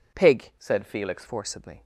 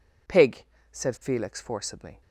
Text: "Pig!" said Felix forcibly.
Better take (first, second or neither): second